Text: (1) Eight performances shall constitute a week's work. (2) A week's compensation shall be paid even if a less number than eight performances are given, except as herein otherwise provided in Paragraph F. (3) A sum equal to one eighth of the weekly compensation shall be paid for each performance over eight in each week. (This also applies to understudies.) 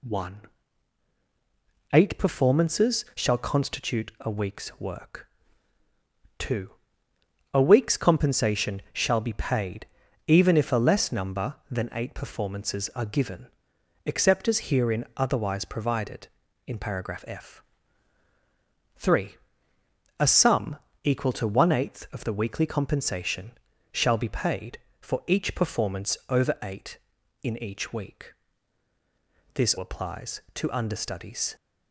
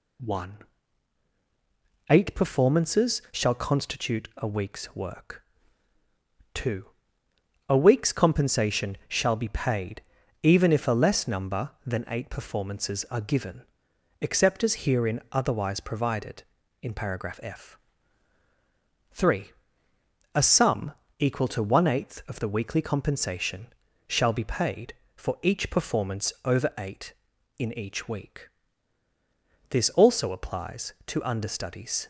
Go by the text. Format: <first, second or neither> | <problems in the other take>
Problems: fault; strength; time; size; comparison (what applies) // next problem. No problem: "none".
second | pauses between "paid" and "even"; at 9.8 s; 0.40 s long; also in the second // pauses between "sum" and "equal"; slight; at 20.7 s; 0.26 s long; slight in the second // pauses between "compensation" and "shall"; at 23.5 s; 0.38 s long; also in the second // skips "also"; at 29.7 s